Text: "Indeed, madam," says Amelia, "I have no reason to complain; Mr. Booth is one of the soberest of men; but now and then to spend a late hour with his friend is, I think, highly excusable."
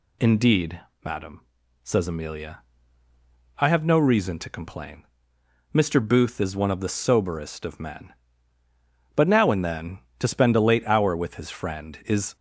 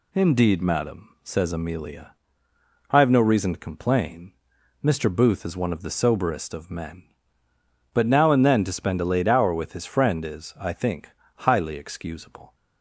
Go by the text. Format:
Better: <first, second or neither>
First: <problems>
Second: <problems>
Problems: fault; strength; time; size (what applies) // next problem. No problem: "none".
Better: second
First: stops before "I think highly excusable"; at 12.3 s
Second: none